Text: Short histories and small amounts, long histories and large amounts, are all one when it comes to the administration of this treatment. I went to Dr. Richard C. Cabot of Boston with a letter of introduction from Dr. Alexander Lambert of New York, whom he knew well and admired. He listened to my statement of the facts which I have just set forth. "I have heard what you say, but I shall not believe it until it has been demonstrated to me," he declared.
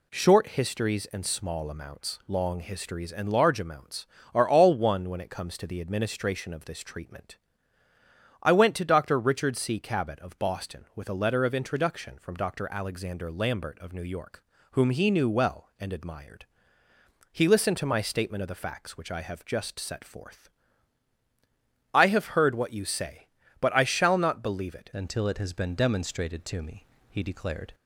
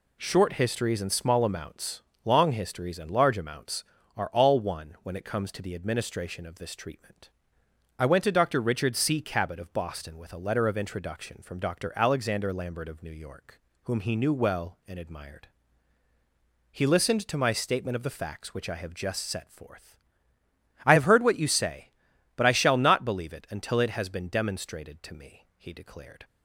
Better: second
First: changes voice at "until"; from 24.9 s on; 2.8 s long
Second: none

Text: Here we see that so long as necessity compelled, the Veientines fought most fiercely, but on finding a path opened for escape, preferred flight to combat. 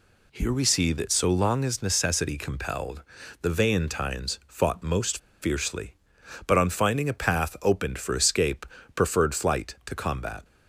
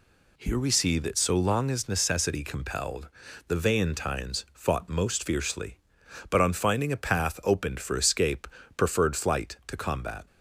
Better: second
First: pauses between "most" and "fiercely"; slight; at 5.1 s; 0.23 s long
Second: none

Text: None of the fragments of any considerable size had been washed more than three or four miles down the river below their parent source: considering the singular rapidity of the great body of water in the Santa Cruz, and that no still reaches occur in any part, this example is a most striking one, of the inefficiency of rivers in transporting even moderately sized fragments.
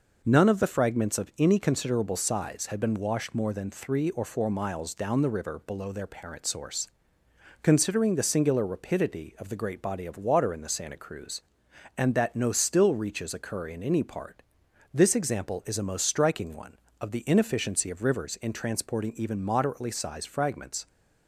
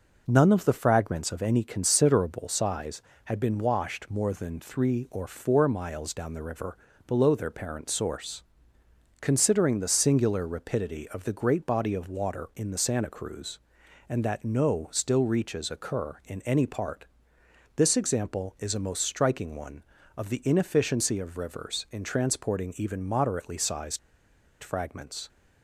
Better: first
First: none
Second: pauses between "river" and "below"; slight; at 6.7 s; 0.30 s long // pauses between "sized" and "fragments"; noticeable; at 23.9 s; 0.64 s long

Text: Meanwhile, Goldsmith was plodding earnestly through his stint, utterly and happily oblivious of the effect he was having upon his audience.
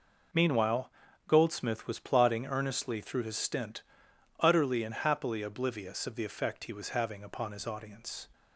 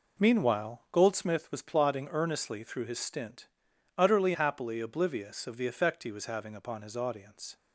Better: first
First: none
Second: skips "and"; at 4.3 s

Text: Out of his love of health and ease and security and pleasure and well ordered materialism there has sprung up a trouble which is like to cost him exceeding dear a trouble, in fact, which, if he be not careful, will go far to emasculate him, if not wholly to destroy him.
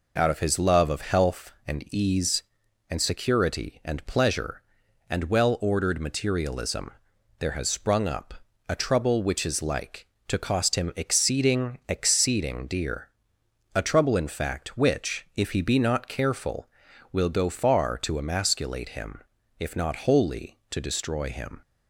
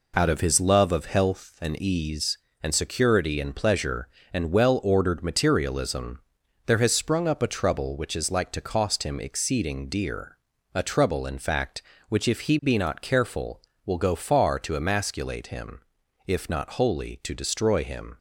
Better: second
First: pauses between "materialism" and "there"; noticeable; at 6.8 s; 0.50 s long // pauses between "up" and "a"; slight; at 8.3 s; 0.34 s long // says "exceeding" twice; at 11.8 s // pauses between "dear" and "a"; noticeable; at 13.0 s; 0.68 s long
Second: pauses between "materialism" and "there"; noticeable; at 6.2 s; 0.46 s long // pauses between "dear" and "a"; noticeable; at 10.3 s; 0.46 s long

